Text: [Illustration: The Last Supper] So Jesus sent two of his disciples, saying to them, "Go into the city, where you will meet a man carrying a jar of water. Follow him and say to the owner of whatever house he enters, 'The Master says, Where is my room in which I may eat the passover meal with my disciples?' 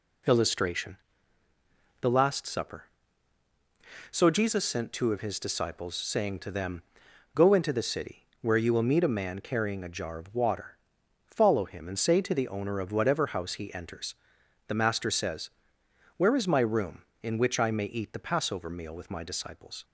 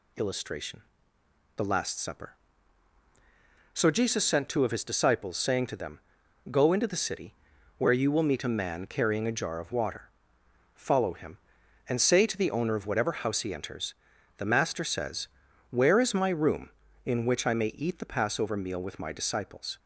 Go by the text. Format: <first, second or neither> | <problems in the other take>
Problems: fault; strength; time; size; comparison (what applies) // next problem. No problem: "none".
neither | none